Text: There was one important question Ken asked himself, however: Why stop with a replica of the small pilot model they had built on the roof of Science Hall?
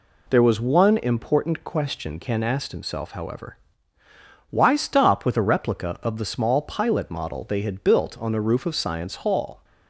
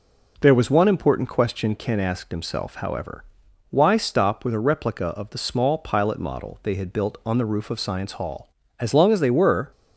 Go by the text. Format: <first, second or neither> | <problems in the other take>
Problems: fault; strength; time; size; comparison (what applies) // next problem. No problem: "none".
first | goes on to say "As long as they were"; noticeable; from 8.8 s on; 0.90 s long